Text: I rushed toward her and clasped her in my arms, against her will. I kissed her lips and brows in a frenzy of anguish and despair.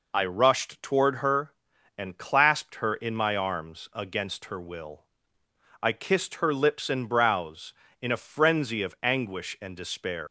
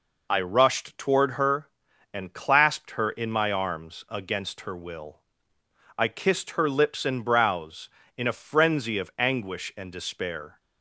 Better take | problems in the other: second | leaves "despair" unfinished; at 10.2 s; 165 ms

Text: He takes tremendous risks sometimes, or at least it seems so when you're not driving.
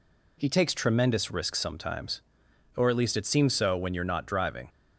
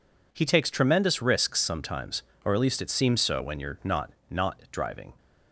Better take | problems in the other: first | says "not" twice; at 4.2 s

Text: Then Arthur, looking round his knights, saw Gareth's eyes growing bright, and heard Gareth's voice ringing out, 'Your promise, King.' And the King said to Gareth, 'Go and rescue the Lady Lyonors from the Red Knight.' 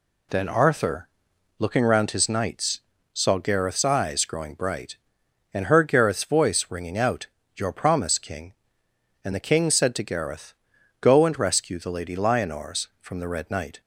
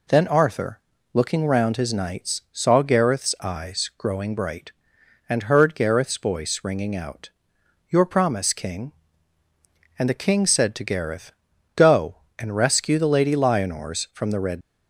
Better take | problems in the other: first | stops before "Knight"; at 14.6 s

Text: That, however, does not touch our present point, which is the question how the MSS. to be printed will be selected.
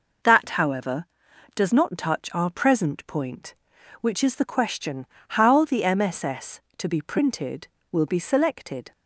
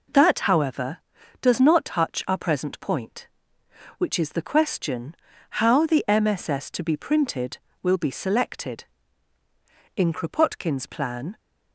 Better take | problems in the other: first | pauses between "question" and "how"; noticeable; at 5.1 s; 0.46 s long; slight in the first // goes on to say "In Kropotkin's plan"; from 9.9 s on; 1.4 s long

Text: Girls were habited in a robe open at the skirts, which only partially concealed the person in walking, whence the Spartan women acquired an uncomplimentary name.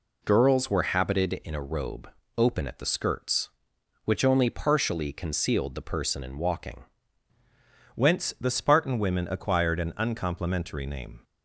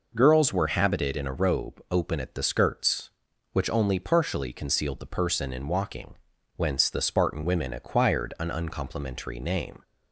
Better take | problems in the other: second | pauses between "robe" and "open"; slight; at 2.0 s; 0.30 s long // changes voice at "whence"; from 7.9 s on; 3.3 s long

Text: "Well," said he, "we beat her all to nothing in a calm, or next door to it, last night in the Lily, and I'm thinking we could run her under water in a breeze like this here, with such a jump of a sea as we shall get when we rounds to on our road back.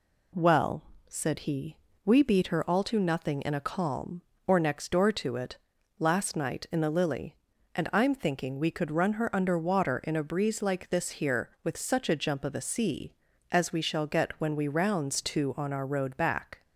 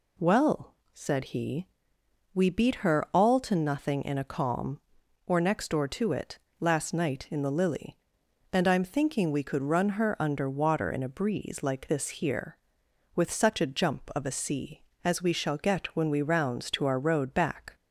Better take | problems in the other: first | skips "on"; at 16.8 s

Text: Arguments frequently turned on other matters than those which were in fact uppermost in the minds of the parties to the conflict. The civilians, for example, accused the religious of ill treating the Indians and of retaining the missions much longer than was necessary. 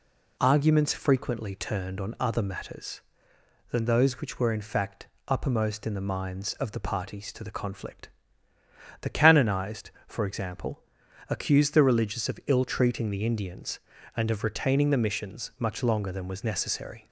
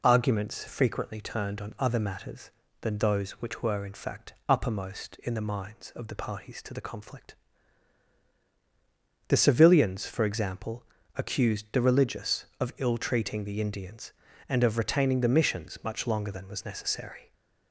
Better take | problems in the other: second | pauses between "fact" and "uppermost"; slight; at 5.0 s; 0.20 s long // says "canonized" for "civilians"; at 9.0 s

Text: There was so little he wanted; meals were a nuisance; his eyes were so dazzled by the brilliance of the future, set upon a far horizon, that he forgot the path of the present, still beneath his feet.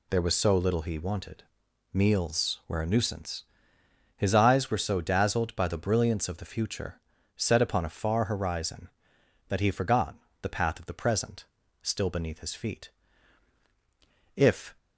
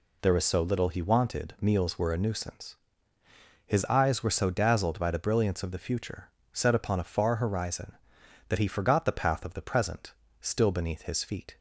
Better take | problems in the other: second | pauses between "forgot" and "the"; slight; at 10.1 s; 0.28 s long // goes on to say "If"; slight; from 14.3 s on; 0.40 s long

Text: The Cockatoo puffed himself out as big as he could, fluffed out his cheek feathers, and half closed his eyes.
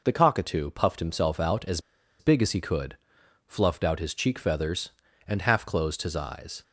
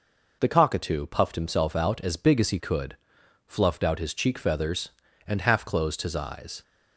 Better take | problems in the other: second | pauses between "as" and "big"; at 1.7 s; 0.40 s long

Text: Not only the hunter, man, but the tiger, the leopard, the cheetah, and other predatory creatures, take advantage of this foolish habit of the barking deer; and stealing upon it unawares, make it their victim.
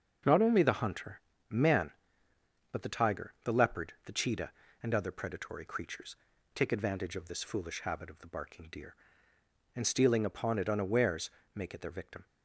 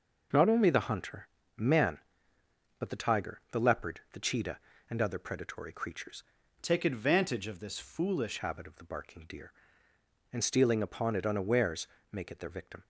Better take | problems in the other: first | changes voice from "take" to "foolish"; from 6.6 to 8.3 s; 1.7 s long

